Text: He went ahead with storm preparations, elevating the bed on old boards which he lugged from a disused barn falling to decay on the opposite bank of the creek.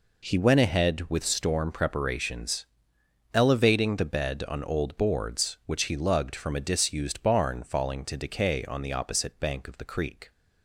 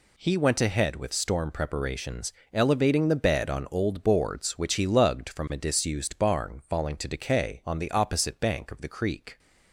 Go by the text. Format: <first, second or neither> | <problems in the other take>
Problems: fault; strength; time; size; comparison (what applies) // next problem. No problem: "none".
neither | none